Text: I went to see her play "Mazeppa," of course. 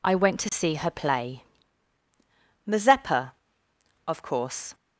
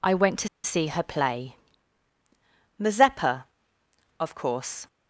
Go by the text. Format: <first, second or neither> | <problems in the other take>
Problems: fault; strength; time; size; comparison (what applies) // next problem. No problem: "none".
first | pauses between "to" and "see"; slight; at 0.4 s; 0.16 s long // pauses between "play" and "Mazeppa"; at 1.5 s; 1.2 s long; also in the first